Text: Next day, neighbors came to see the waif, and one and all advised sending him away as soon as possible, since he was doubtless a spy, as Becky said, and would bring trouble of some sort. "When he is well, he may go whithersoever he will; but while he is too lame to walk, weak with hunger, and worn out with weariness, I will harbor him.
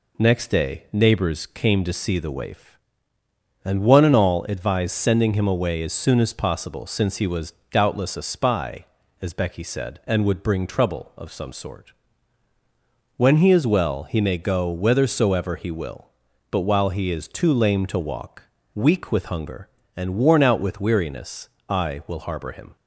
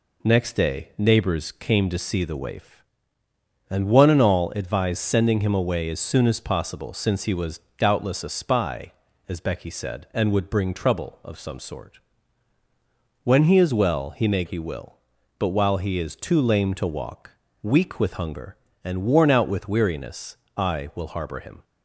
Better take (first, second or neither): first